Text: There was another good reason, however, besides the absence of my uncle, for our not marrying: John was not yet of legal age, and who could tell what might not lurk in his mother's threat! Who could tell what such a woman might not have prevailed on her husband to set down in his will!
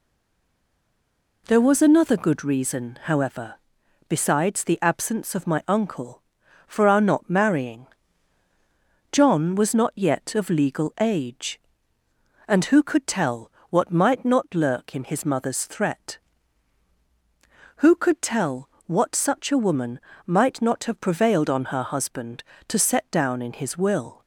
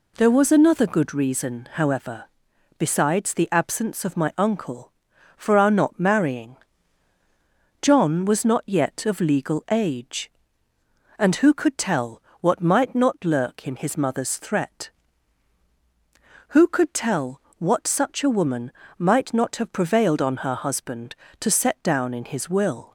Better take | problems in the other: second | stays silent before the first word; noticeable; until 1.4 s; 1.4 s long // pauses between "tell" and "what"; slight; at 13.5 s; 0.20 s long; slight in the second // pauses between "tell" and "what"; slight; at 18.6 s; 0.16 s long; slight in the second // pauses between "woman" and "might"; slight; at 19.9 s; 0.28 s long; slight in the second

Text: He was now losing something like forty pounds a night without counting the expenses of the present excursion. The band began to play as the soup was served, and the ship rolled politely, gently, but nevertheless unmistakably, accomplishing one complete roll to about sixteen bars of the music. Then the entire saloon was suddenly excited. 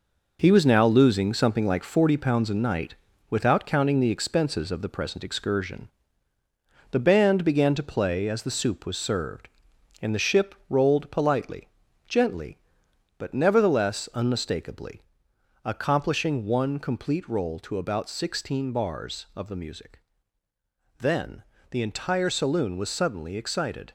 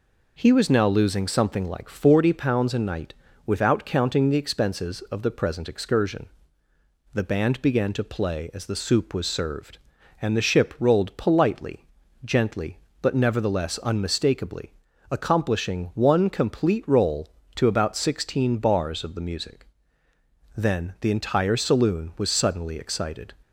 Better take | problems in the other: second | gets quieter; strong; throughout; 7 dB // pauses between "night" and "without"; slight; at 2.9 s; 0.34 s long; slight in the second // pauses between "ship" and "rolled"; slight; at 10.5 s; 0.16 s long // pauses between "Then" and "the"; slight; at 21.4 s; 0.26 s long

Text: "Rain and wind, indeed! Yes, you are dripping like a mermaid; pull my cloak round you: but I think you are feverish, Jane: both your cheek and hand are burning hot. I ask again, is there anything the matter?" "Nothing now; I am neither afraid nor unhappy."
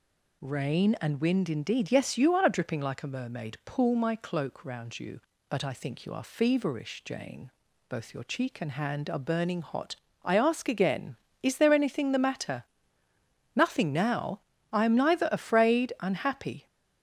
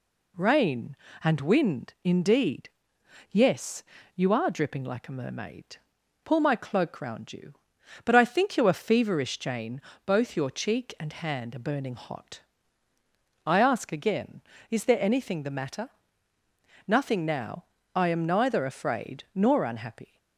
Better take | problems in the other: second | skips "nor"; at 15.9 s

